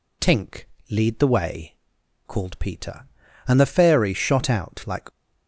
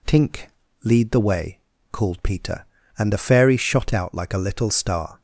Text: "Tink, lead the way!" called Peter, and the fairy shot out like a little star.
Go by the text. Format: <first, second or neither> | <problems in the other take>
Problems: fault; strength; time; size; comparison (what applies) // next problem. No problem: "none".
second | stops before "a little star"; at 5.0 s